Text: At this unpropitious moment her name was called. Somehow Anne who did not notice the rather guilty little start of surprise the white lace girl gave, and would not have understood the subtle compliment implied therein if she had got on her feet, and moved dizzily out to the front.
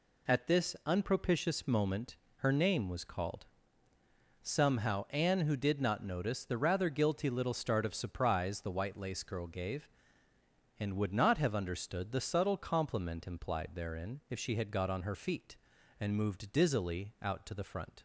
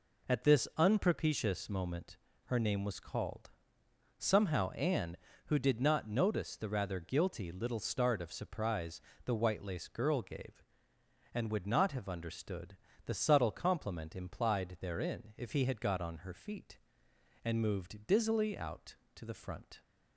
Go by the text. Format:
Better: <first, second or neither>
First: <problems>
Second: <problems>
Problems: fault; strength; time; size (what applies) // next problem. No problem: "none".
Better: first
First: pauses between "moment" and "her"; slight; at 2.1 s; 0.22 s long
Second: pauses between "moment" and "her"; slight; at 2.1 s; 0.28 s long // pauses between "surprise" and "the"; slight; at 9.0 s; 0.24 s long // pauses between "understood" and "the"; slight; at 12.7 s; 0.28 s long // says "he" for "she"; at 15.5 s